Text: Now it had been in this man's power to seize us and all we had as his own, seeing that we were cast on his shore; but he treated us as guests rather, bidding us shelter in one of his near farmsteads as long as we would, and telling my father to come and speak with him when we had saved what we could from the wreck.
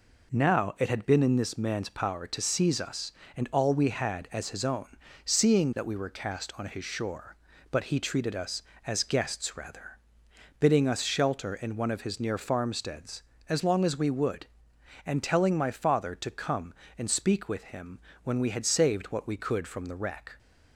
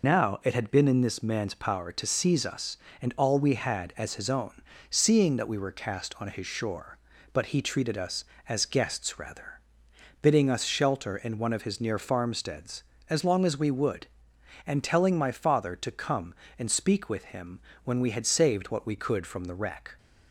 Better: first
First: pauses between "him" and "when"; slight; at 17.9 s; 0.24 s long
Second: loses the start of "Now"; at 0.0 s; 75 ms // pauses between "him" and "when"; slight; at 17.6 s; 0.24 s long

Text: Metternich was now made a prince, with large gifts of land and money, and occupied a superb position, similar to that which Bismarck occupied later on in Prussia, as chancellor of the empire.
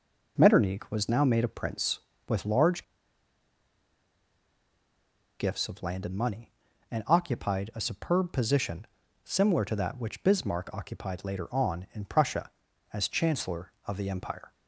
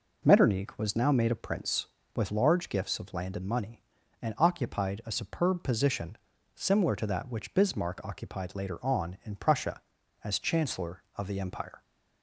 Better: second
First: pauses between "large" and "gifts"; strong; at 2.8 s; 2.5 s long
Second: none

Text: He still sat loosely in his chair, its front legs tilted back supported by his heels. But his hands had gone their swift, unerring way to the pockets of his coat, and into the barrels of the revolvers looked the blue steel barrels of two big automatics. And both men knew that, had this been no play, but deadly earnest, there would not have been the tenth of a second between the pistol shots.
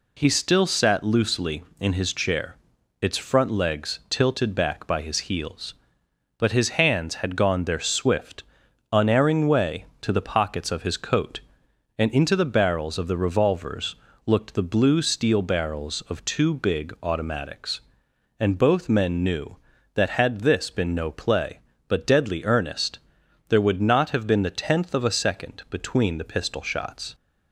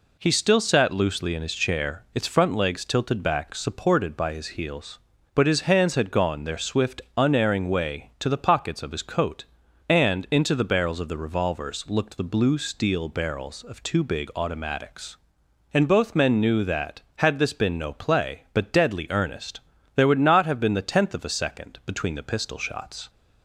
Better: second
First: skips "supported"; at 4.8 s // pauses between "revolvers" and "looked"; slight; at 13.9 s; 0.32 s long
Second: none

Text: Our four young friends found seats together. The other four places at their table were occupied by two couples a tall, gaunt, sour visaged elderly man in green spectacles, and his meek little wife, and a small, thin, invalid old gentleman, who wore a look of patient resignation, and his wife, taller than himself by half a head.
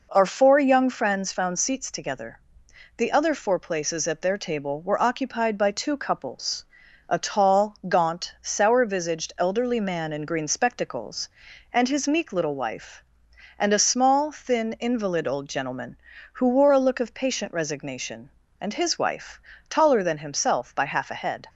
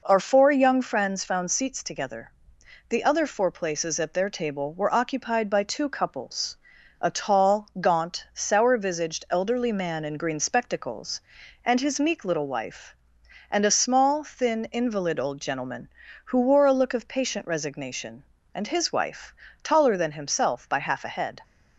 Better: neither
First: pauses between "couples" and "a"; noticeable; at 6.6 s; 0.46 s long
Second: pauses between "couples" and "a"; noticeable; at 6.5 s; 0.46 s long

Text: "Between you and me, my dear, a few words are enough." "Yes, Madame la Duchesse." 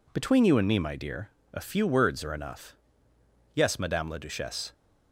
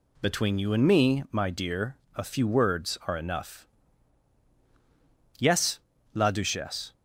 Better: first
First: none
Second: skips "Madame"; at 5.9 s

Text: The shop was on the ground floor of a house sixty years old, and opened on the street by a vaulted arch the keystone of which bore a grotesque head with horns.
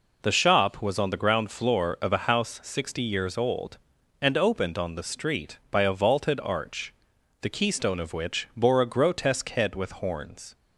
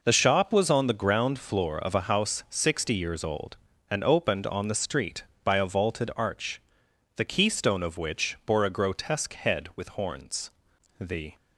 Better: first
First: pauses between "arch" and "the"; noticeable; at 6.9 s; 0.48 s long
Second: pauses between "arch" and "the"; noticeable; at 6.5 s; 0.58 s long // goes on to say "The"; slight; from 10.9 s on; 0.36 s long

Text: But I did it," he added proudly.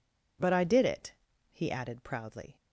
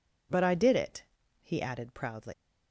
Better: first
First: none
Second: leaves "proudly" unfinished; at 2.3 s; 125 ms

